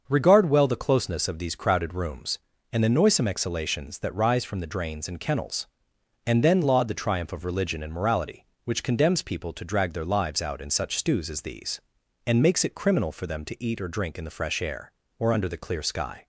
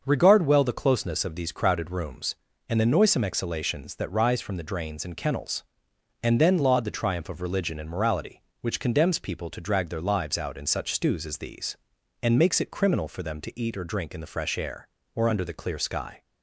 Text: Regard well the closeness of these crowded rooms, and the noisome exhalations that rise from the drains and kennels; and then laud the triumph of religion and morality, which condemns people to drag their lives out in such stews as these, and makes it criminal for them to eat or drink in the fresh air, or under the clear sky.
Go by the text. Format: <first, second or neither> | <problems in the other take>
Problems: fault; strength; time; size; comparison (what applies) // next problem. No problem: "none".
neither | starts louder than the rest; the same in both